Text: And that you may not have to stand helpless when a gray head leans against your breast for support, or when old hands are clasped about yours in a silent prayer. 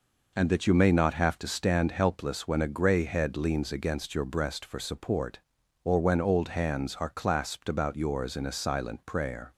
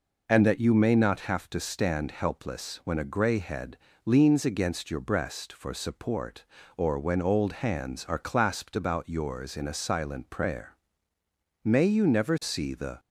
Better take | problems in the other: first | pauses between "head" and "leans"; slight; at 3.7 s; 0.26 s long // goes on to say "May you never see the"; from 11.6 s on; 1.3 s long

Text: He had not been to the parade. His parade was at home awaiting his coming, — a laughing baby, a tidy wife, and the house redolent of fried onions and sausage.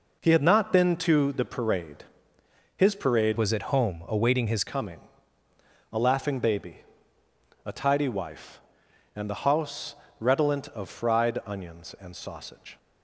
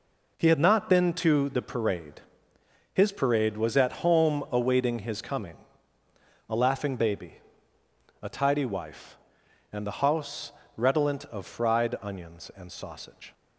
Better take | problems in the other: second | changes voice from "was" to "his"; from 3.3 to 4.6 s; 1.3 s long // pauses between "house" and "redolent"; slight; at 9.9 s; 0.24 s long; slight in the second

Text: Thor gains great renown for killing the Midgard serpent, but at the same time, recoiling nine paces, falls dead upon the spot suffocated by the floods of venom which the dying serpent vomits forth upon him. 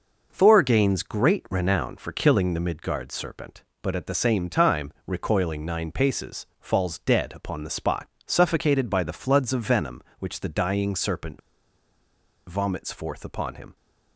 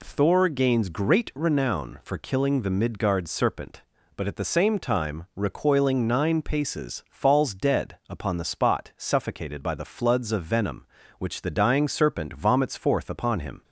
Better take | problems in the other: second | pauses between "spot" and "suffocated"; slight; at 8.0 s; 0.20 s long // pauses between "serpent" and "vomits"; at 11.3 s; 1.0 s long

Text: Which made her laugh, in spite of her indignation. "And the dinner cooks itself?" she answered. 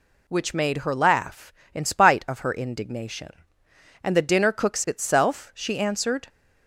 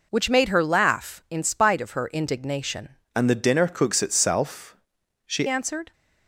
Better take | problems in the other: first | changes voice from "And" to "she"; from 3.1 to 5.4 s; 2.3 s long

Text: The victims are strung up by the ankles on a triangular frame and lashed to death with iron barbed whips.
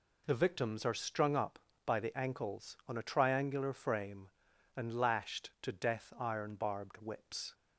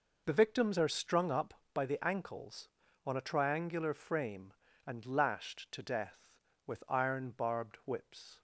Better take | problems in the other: second | skips "with"; at 6.1 s

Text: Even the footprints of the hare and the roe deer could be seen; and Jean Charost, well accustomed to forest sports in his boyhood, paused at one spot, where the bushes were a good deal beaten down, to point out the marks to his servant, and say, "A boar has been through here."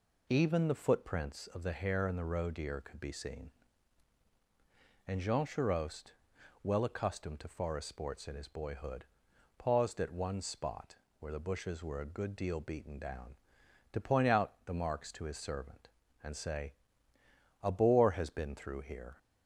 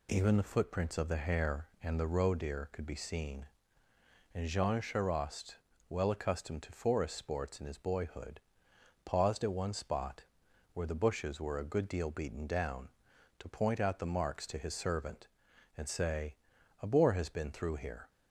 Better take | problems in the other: neither | none

